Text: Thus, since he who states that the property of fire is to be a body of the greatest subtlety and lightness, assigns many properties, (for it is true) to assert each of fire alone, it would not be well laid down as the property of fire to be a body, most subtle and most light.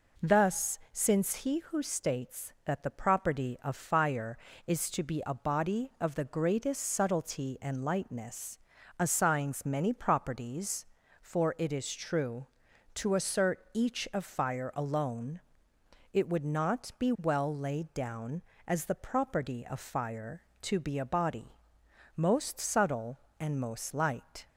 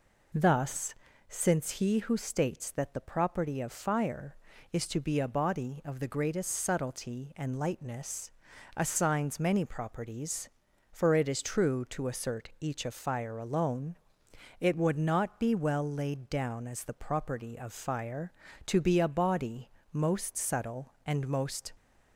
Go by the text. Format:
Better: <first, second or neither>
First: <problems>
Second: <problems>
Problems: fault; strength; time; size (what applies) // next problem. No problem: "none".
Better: first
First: none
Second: stops before "light"; at 21.7 s